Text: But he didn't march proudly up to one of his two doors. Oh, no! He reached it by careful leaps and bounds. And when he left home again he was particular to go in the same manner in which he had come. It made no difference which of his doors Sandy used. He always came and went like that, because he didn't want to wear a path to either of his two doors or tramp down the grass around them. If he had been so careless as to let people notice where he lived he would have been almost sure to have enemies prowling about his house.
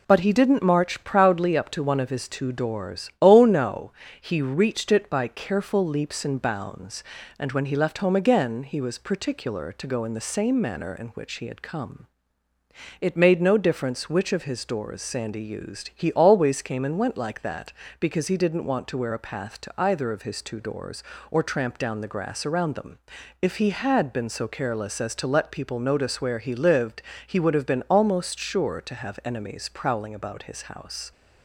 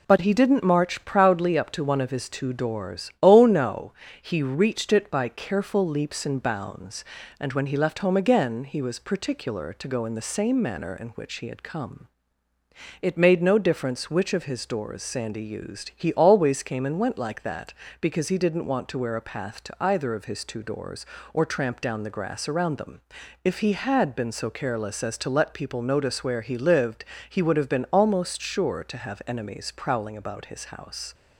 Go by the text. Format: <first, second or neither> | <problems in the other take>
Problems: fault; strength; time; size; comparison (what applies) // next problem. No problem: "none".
neither | pauses between "lived" and "he"; slight; the same in both